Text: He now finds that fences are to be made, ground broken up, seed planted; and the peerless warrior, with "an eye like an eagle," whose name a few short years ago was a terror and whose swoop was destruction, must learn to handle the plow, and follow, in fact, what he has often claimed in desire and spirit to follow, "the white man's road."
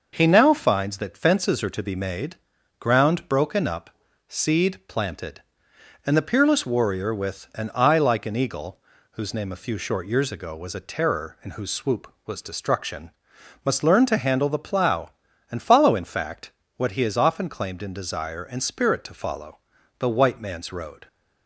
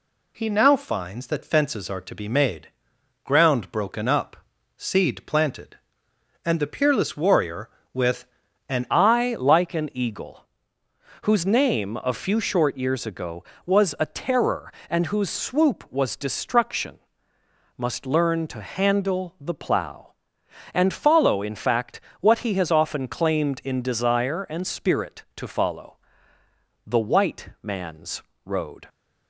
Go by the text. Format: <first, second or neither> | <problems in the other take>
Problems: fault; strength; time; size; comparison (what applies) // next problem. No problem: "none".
first | pauses between "with" and "an"; at 8.2 s; 0.42 s long // changes voice at "eye"; from 8.9 s on; 19.9 s long // pauses between "man's" and "road"; slight; at 28.2 s; 0.22 s long